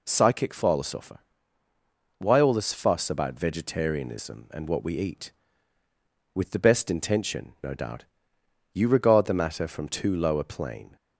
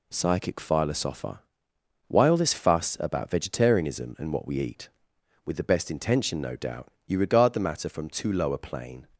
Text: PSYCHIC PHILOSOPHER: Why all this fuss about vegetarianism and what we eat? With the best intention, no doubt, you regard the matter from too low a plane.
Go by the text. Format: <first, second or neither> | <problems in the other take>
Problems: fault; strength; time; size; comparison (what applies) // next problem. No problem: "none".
neither | none